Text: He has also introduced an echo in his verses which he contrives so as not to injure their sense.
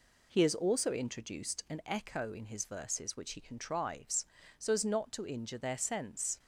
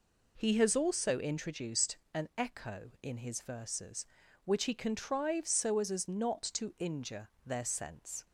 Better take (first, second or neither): first